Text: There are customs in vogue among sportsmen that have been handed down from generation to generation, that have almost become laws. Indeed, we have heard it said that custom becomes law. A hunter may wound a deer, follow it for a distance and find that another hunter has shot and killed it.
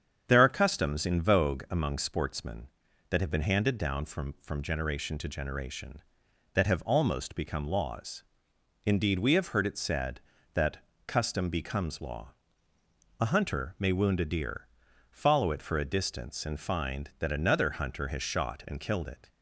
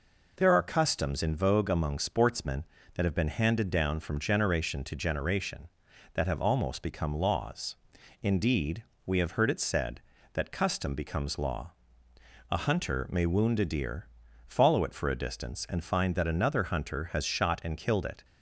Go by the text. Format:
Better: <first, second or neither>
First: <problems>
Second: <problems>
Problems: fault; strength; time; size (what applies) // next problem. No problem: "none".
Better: second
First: starts louder than the rest; strong; until 1.2 s; 7.5 dB // says "from" twice; at 4.4 s // pauses between "that" and "custom"; slight; at 10.7 s; 0.30 s long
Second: none